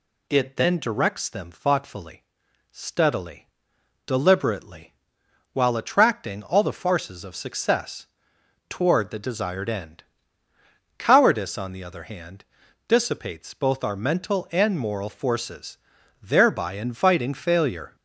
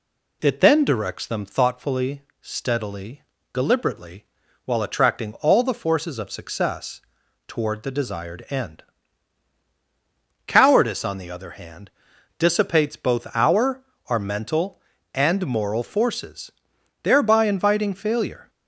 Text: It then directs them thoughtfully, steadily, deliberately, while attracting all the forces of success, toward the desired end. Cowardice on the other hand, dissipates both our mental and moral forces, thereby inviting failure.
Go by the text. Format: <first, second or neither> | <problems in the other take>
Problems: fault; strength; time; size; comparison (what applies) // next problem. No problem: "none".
first | says "our" twice; at 14.0 s